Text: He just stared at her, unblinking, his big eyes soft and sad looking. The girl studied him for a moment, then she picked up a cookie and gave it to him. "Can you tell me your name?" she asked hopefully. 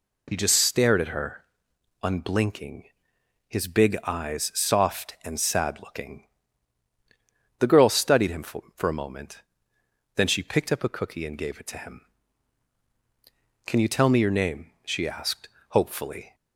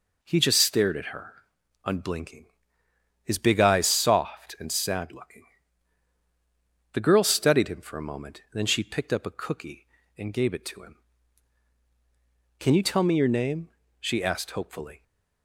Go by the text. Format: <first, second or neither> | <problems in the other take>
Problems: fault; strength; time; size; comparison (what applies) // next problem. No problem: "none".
second | says "for" twice; at 8.7 s // pauses between "asked" and "hopefully"; slight; at 15.4 s; 0.20 s long